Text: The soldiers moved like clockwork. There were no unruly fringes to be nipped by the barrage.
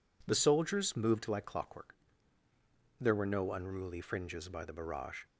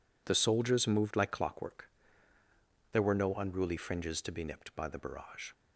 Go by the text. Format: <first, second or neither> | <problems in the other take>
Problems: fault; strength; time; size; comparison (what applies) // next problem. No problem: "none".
second | skips "to be nipped"; at 4.4 s